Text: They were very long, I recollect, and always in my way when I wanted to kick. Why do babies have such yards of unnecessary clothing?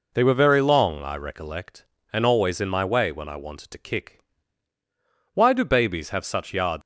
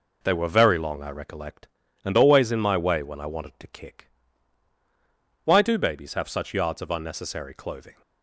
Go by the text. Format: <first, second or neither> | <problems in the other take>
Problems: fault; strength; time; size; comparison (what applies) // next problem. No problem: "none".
second | stops before "of unnecessary clothing"; at 6.8 s